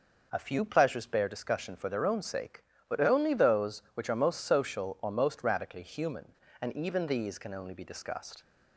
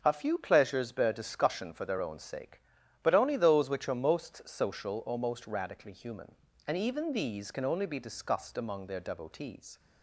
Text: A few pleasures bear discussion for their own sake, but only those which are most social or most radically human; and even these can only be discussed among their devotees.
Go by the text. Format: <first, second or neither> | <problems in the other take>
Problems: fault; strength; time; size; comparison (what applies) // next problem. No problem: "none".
second | stops before "among their devotees"; at 8.4 s